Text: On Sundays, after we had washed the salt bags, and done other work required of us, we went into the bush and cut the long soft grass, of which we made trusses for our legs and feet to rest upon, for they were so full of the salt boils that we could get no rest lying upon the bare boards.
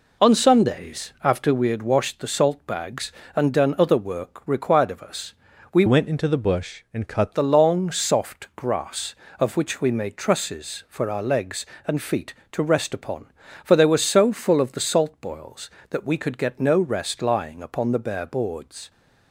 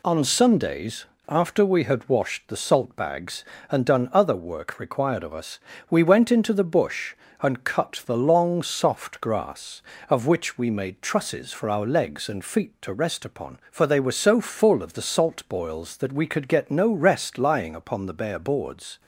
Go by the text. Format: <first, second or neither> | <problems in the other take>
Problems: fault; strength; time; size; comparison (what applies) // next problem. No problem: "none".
second | changes voice from "went" to "cut"; from 5.8 to 7.3 s; 1.5 s long